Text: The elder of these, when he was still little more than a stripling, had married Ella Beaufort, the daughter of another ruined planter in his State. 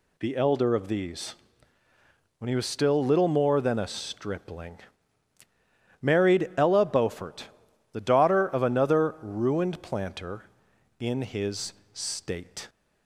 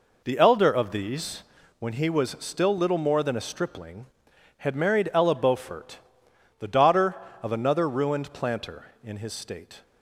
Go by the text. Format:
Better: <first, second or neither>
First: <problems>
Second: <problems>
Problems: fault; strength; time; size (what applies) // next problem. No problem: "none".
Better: second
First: skips "had"; at 5.4 s // pauses between "his" and "State"; slight; at 11.7 s; 0.18 s long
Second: none